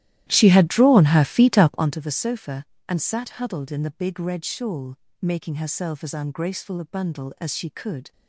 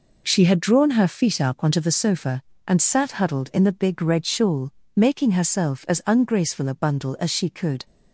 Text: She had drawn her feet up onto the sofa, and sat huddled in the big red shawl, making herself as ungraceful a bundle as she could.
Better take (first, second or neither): second